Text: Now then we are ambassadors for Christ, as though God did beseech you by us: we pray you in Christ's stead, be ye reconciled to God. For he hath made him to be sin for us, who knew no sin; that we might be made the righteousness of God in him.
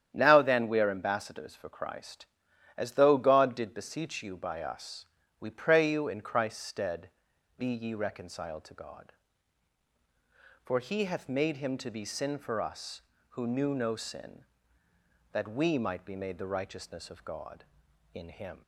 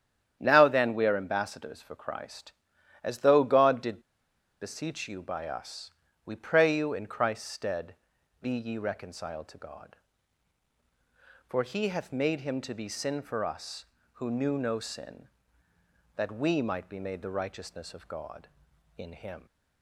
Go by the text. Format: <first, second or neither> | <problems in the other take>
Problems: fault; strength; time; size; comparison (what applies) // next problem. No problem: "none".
first | starts louder than the rest; strong; until 1.4 s; 9.5 dB; strong in the first // pauses between "did" and "beseech"; noticeable; at 4.0 s; 0.61 s long